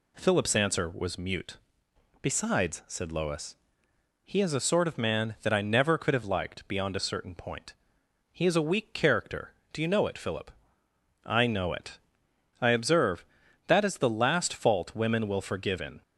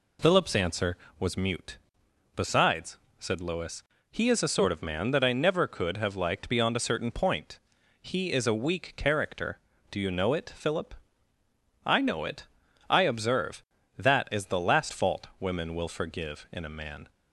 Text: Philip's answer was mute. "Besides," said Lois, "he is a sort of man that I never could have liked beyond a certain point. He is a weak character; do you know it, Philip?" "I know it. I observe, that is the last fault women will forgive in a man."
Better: second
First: stops before "a man"; at 16.0 s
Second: none

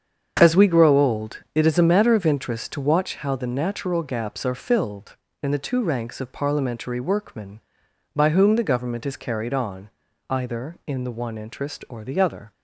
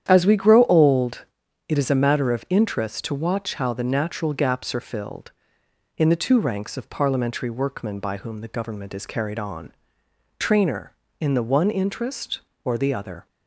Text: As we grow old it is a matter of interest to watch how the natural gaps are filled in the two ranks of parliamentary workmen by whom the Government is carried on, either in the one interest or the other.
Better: first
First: starts louder than the rest; strong; until 1.4 s; 7.5 dB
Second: starts louder than the rest; strong; until 1.1 s; 9.5 dB // pauses between "old" and "it"; at 1.2 s; 0.42 s long // says "trainer" for "either"; at 10.3 s

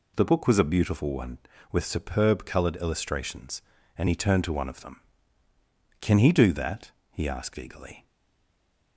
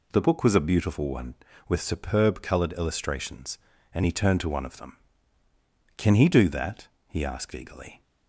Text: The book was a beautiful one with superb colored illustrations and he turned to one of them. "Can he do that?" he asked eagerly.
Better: second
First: stays silent after the last word; slight; from 8.0 s on; 0.9 s long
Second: none

